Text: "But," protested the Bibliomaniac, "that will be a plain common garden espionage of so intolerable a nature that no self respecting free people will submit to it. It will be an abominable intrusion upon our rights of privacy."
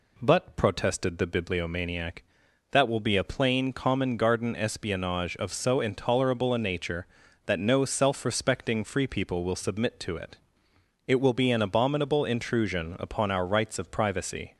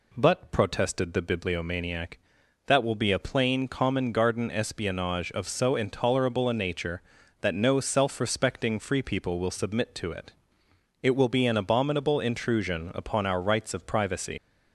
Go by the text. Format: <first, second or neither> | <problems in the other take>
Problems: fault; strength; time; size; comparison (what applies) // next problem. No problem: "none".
first | leaves "privacy" unfinished; at 14.3 s; 125 ms